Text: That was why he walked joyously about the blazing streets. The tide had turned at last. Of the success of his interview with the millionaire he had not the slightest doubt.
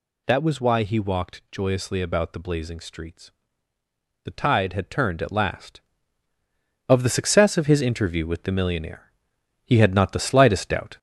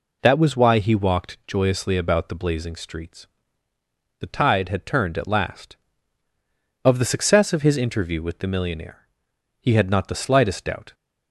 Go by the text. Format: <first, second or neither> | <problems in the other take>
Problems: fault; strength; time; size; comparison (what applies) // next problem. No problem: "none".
second | gets louder; noticeable; throughout; 4.5 dB // pauses between "millionaire" and "he"; noticeable; at 9.0 s; 0.56 s long; noticeable in the second